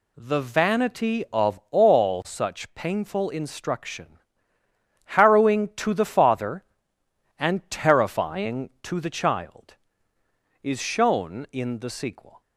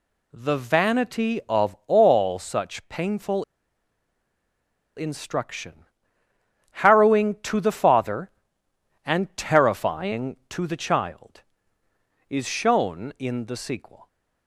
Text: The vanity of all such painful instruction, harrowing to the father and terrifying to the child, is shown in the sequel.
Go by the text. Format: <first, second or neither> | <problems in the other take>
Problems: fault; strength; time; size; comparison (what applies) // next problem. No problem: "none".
first | pauses between "painful" and "instruction"; strong; at 3.4 s; 1.5 s long